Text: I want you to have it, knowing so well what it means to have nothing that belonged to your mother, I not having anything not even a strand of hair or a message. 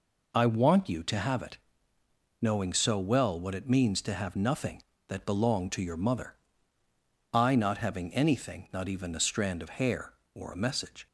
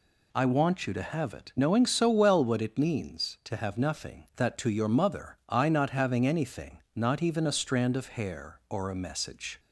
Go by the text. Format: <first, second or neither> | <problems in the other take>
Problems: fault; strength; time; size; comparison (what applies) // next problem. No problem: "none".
first | skips "belonged"; at 4.5 s // pauses between "anything" and "not"; slight; at 6.7 s; 0.18 s long